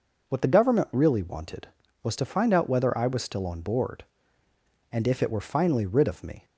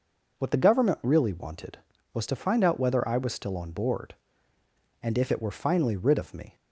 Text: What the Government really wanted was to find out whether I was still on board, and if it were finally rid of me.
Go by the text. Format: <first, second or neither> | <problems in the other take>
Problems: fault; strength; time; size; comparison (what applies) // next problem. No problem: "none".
neither | none